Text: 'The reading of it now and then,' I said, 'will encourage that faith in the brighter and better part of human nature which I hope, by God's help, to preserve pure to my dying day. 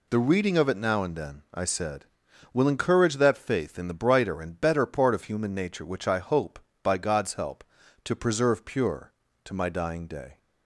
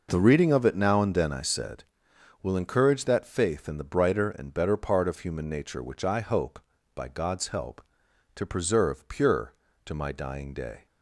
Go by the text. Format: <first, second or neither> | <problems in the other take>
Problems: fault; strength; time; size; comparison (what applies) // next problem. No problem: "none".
neither | none